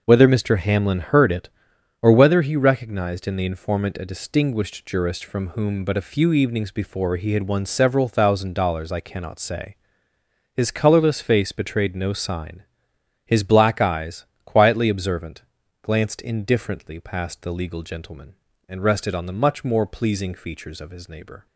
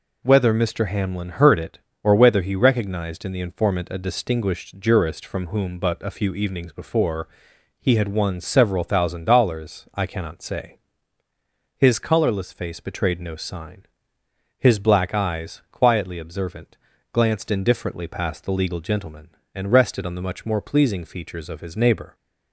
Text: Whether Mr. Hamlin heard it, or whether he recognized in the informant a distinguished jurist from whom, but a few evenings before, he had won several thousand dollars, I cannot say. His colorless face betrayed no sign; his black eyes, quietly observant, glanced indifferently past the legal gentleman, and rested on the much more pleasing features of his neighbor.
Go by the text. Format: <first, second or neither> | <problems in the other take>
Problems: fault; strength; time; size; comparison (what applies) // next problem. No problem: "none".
neither | none